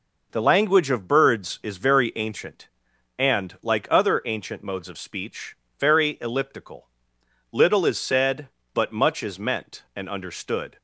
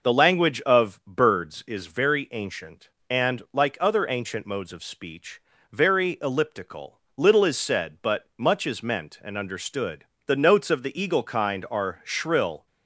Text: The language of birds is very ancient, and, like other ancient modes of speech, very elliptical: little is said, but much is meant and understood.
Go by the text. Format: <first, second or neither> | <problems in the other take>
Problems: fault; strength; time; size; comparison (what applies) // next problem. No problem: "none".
first | goes on to say "The notes of the eagle kind are shrill"; strong; from 10.2 s on; 2.3 s long